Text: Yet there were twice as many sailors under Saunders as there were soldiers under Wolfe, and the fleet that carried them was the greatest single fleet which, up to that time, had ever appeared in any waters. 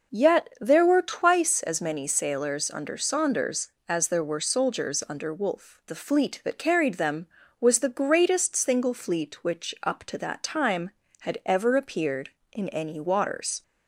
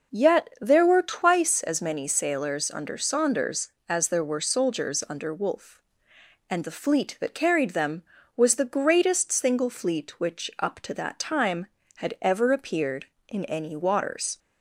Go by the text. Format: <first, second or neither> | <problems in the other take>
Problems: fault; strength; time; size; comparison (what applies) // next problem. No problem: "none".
second | skips "and"; at 5.8 s